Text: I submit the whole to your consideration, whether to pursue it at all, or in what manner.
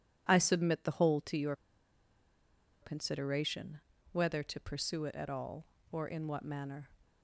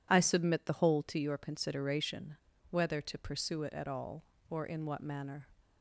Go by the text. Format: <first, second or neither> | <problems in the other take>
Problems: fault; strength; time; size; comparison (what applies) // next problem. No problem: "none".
second | pauses between "your" and "consideration"; strong; at 1.5 s; 1.2 s long